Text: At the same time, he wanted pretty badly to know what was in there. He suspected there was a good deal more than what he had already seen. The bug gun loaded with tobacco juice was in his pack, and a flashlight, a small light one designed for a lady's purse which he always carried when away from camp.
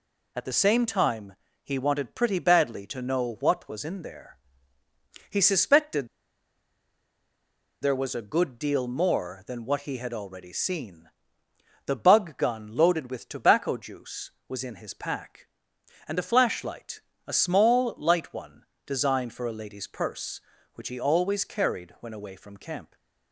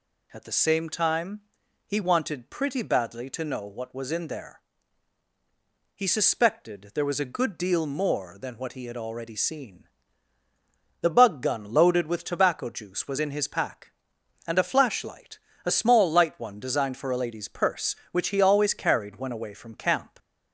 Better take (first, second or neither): second